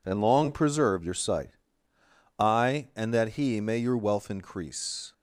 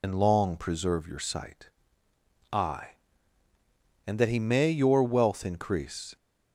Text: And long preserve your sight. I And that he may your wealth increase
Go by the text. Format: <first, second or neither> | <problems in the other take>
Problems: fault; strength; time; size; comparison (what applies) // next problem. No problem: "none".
first | loses the start of "And"; at 0.0 s; 50 ms